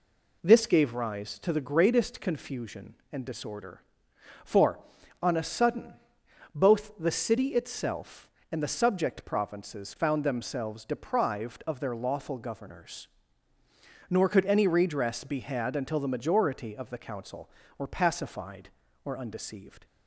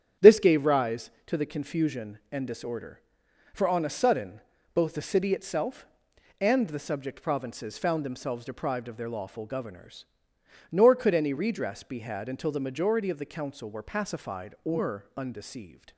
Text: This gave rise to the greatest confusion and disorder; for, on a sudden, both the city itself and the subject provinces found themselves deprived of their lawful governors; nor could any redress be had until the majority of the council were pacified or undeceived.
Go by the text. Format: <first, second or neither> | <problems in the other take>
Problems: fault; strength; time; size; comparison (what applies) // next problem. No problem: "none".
first | starts louder than the rest; strong; until 1.3 s; 9 dB // skips "greatest"; at 1.4 s